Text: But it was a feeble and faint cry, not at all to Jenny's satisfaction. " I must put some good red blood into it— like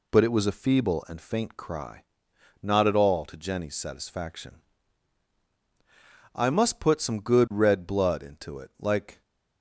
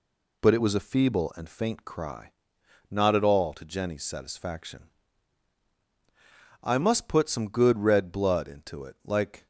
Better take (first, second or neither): neither